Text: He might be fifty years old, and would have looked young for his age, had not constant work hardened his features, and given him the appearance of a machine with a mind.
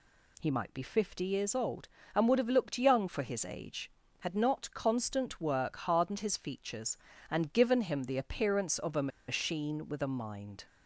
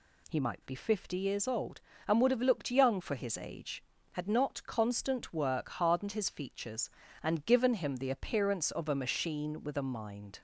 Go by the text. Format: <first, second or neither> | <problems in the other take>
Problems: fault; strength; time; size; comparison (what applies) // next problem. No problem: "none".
second | pauses between "a" and "machine"; slight; at 9.0 s; 0.20 s long